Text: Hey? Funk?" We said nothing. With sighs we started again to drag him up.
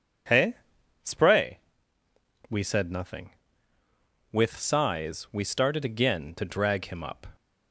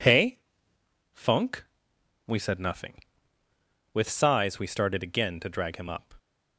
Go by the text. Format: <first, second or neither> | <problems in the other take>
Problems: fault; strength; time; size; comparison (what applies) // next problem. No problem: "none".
second | says "Spray" for "Funk"; at 1.0 s